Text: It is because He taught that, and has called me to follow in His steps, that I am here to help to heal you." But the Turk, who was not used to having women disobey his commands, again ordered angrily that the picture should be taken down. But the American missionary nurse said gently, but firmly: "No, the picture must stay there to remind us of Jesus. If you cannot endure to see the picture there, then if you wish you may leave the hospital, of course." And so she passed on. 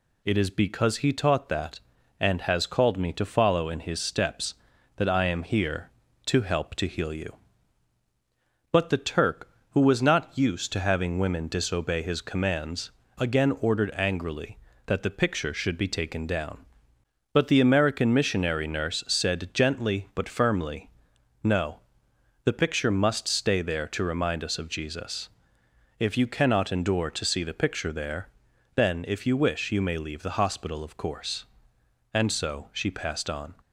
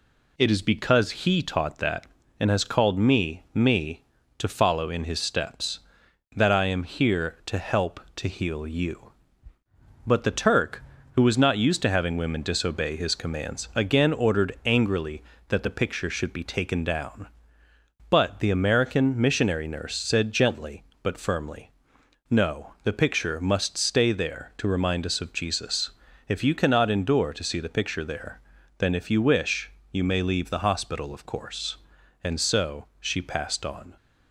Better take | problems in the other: first | says "me" twice; at 3.5 s // pauses between "wish" and "you"; slight; at 29.6 s; 0.22 s long

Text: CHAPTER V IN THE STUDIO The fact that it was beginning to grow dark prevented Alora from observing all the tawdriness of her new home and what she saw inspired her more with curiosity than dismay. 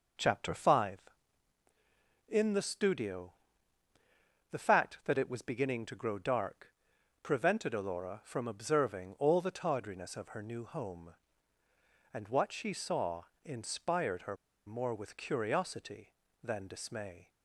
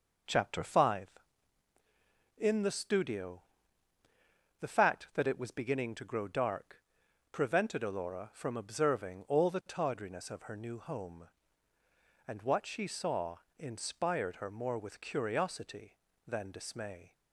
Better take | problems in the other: second | pauses between "STUDIO" and "The"; at 3.3 s; 1.1 s long; also in the second // pauses between "dark" and "prevented"; noticeable; at 6.6 s; 0.56 s long; noticeable in the second // pauses between "saw" and "inspired"; slight; at 13.2 s; 0.20 s long; slight in the second // pauses between "her" and "more"; slight; at 14.3 s; 0.30 s long

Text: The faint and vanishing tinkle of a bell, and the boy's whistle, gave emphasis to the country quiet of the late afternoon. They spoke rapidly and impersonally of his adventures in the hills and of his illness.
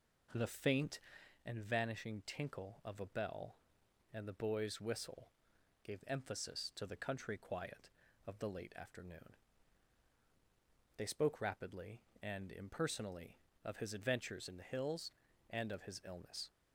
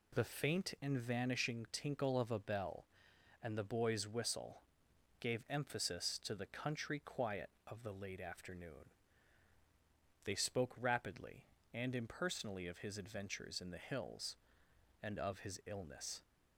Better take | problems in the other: second | starts louder than the rest; noticeable; until 1.4 s; 4.5 dB

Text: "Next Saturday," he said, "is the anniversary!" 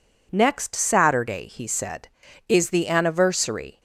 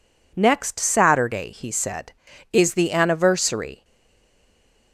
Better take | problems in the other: first | stays silent after the last word; from 3.8 s on; 1.1 s long

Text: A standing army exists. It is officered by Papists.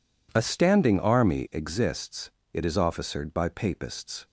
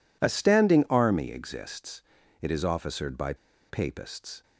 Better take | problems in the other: first | pauses between "by" and "Papists"; slight; at 3.3 s; 0.34 s long

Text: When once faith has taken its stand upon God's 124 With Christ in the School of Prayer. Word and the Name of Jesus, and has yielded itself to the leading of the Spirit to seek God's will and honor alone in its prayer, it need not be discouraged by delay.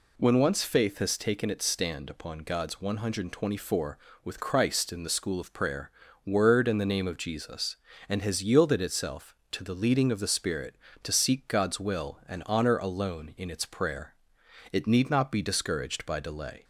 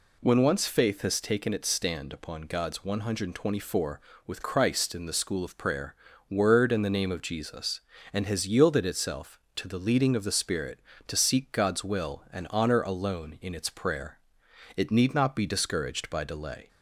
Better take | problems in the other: neither | none

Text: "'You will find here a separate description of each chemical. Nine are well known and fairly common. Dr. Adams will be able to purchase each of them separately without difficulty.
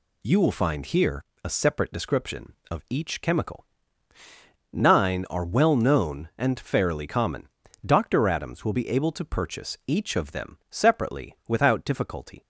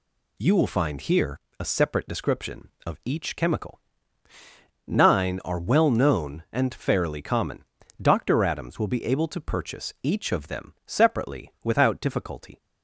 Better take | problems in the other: neither | pauses between "here" and "a"; slight; the same in both

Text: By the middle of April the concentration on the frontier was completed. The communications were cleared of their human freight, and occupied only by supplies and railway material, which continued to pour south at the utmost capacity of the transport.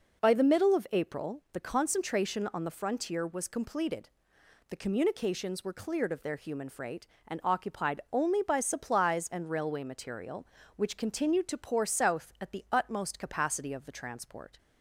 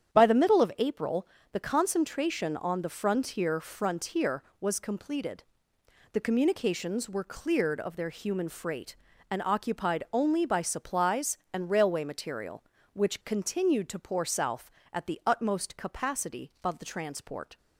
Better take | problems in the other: first | starts louder than the rest; strong; until 1.1 s; 9 dB // pauses between "April" and "the"; slight; at 1.2 s; 0.28 s long // says "frontier" twice; at 3.6 s

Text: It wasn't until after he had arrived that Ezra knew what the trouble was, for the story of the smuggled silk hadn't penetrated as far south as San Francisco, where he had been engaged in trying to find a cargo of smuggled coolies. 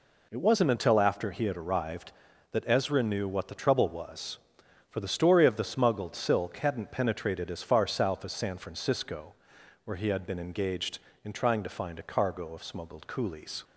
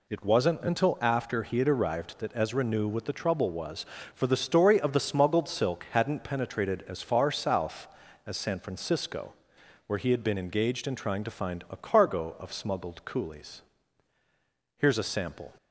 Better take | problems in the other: first | goes on to say "Here's a sample"; noticeable; from 14.7 s on; 0.74 s long

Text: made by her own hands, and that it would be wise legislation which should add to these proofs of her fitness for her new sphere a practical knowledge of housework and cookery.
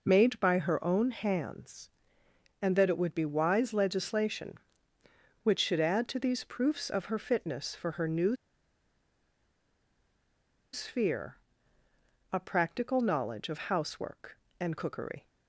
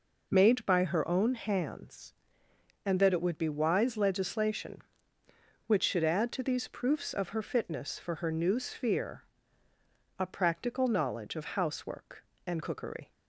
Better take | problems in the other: second | pauses between "new" and "sphere"; strong; at 8.3 s; 2.3 s long // pauses between "sphere" and "a"; noticeable; at 11.3 s; 0.96 s long; noticeable in the second

